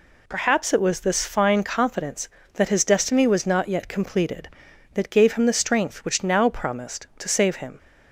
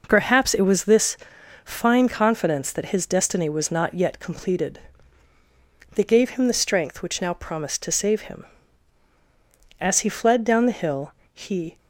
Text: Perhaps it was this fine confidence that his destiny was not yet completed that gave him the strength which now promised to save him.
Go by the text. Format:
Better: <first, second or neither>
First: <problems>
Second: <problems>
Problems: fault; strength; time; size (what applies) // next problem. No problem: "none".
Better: first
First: none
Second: pauses between "this" and "fine"; noticeable; at 1.1 s; 0.46 s long // goes on to say "As he fled down the hill he"; strong; from 9.7 s on; 1.9 s long